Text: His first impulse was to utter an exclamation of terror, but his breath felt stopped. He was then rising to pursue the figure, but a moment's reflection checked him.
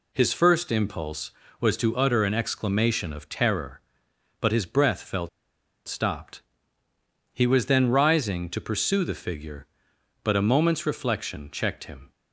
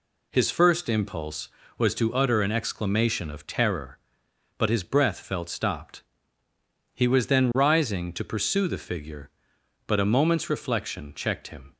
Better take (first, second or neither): second